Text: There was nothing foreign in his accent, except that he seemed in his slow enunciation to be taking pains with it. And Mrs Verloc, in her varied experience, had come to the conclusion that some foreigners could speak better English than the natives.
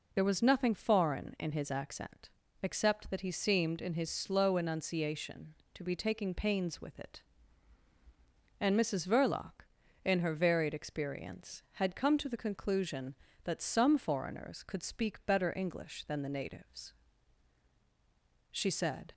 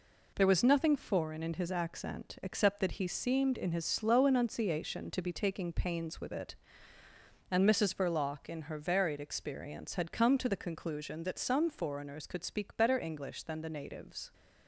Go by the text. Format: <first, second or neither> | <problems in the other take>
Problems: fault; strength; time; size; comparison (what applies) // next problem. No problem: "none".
second | goes on to say "She said"; noticeable; from 18.5 s on; 0.62 s long